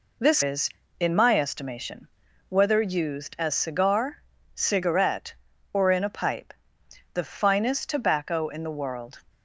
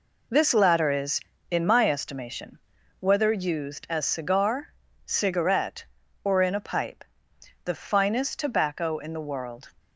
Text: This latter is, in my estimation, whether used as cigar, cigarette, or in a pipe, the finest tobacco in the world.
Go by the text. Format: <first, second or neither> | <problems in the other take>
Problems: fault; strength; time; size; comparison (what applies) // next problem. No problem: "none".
second | skips "latter"; at 0.4 s